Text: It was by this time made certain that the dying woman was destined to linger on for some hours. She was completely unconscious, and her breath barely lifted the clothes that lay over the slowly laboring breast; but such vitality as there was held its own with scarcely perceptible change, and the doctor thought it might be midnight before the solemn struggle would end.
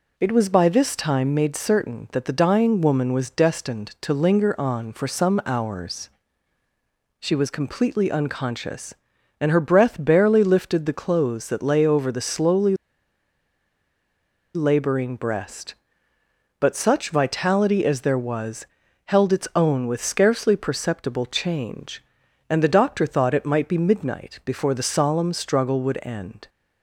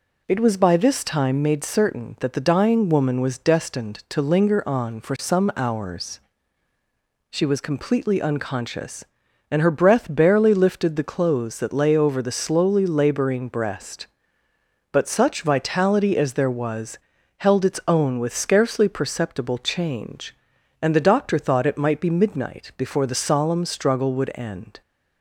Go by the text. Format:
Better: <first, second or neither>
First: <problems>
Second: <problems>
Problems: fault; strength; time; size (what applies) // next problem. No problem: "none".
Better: second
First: pauses between "slowly" and "laboring"; strong; at 12.7 s; 1.8 s long // pauses between "was" and "held"; at 18.6 s; 0.38 s long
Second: pauses between "was" and "held"; at 16.9 s; 0.38 s long